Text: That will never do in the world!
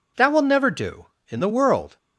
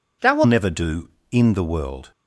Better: first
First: none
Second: changes voice at "never"; from 0.4 s on; 1.7 s long

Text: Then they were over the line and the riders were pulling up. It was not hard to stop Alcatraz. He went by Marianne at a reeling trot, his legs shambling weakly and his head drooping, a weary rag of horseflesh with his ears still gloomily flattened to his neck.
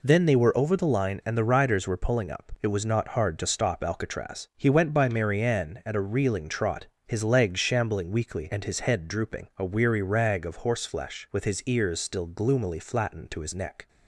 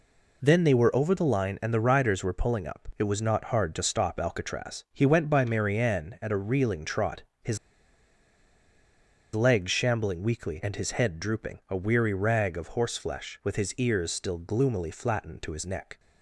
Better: first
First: none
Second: pauses between "his" and "legs"; strong; at 7.5 s; 1.7 s long

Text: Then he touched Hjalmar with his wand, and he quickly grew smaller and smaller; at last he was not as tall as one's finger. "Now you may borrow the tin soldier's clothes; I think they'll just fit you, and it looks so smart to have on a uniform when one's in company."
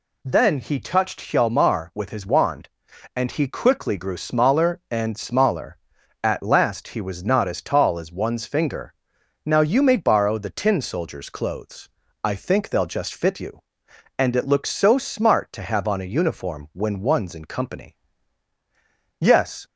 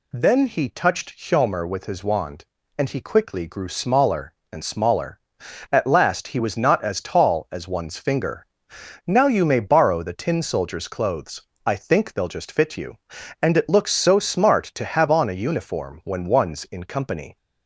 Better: second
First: goes on to say "Yes"; slight; from 19.1 s on; 0.48 s long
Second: none

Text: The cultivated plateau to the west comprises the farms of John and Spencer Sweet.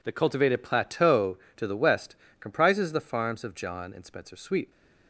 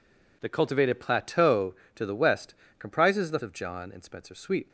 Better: first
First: pauses between "west" and "comprises"; slight; at 2.1 s; 0.26 s long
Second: pauses between "west" and "comprises"; slight; at 2.5 s; 0.26 s long // skips "farms"; at 3.4 s

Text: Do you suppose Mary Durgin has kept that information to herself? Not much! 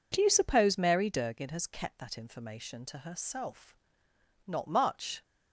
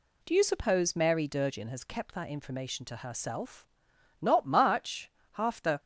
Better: first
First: none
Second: goes on to say "Half the"; slight; from 5.3 s on; 0.48 s long

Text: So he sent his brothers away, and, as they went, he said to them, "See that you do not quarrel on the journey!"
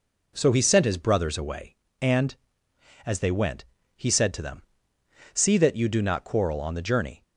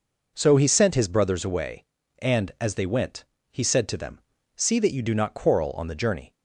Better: neither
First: none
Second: none

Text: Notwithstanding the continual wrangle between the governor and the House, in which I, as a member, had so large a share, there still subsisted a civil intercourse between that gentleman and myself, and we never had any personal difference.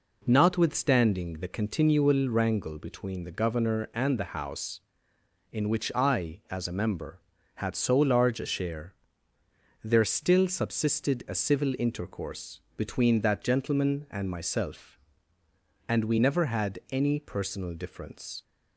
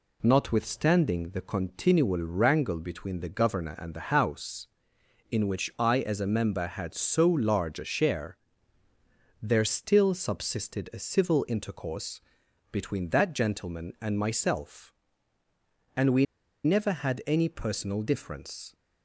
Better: first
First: pauses between "intercourse" and "between"; slight; at 12.6 s; 0.16 s long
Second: pauses between "intercourse" and "between"; noticeable; at 12.2 s; 0.50 s long // pauses between "we" and "never"; at 16.2 s; 0.41 s long

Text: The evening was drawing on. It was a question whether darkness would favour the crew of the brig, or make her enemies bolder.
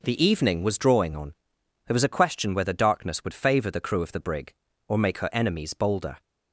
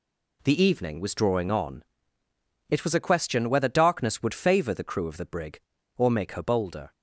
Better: first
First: none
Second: skips "enemies"; at 6.4 s

